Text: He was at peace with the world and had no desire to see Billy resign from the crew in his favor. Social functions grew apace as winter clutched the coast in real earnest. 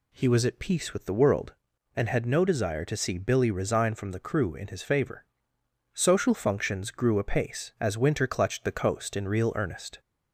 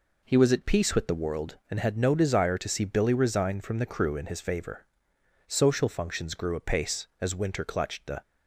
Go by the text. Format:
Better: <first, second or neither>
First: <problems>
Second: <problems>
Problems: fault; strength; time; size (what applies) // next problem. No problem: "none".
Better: first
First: none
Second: stops before "coast in real earnest"; at 8.2 s